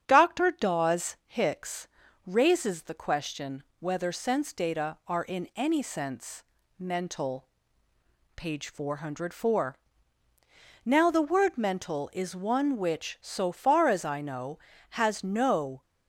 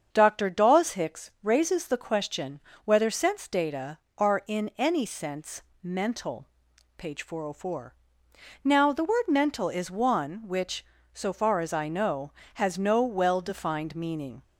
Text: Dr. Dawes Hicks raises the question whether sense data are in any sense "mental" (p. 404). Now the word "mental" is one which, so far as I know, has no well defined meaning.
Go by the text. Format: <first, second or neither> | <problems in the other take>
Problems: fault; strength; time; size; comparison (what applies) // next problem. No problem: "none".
second | starts louder than the rest; strong; until 1.0 s; 8.5 dB; also in the second // pauses between "Hicks" and "raises"; at 1.8 s; 0.40 s long // pauses between "question" and "whether"; slight; at 3.6 s; 0.16 s long; slight in the second // pauses between "sense" and "mental"; slight; at 6.4 s; 0.34 s long; slight in the second // stops before "well defined meaning"; at 15.8 s